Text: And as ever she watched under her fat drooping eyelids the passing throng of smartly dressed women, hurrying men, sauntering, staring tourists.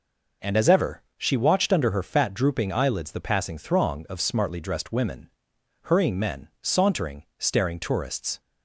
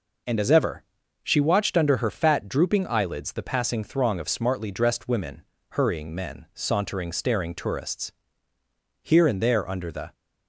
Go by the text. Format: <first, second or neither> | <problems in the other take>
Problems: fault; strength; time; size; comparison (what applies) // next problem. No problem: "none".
first | pauses between "ever" and "she"; at 0.8 s; 0.38 s long; slight in the first // goes on to say "Here and there under the"; noticeable; from 9.0 s on; 1.1 s long